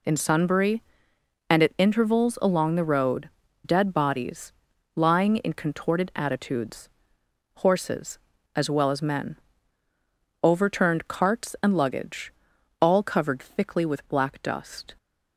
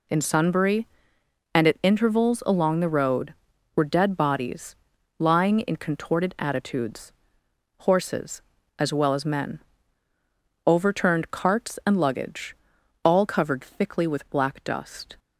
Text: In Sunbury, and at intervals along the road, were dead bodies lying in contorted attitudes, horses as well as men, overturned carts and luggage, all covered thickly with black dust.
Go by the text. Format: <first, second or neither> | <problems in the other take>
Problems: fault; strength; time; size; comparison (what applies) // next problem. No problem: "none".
second | skips "were"; at 3.4 s // pauses between "bodies" and "lying"; at 4.5 s; 0.42 s long; also in the second